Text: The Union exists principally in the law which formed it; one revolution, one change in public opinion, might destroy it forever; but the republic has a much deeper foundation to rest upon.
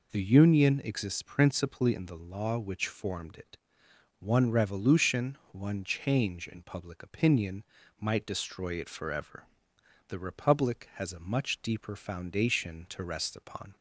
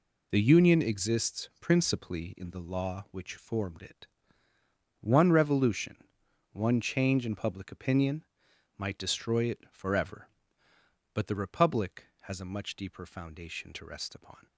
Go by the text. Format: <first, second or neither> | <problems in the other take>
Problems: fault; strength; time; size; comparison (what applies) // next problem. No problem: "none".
second | skips "but"; at 9.7 s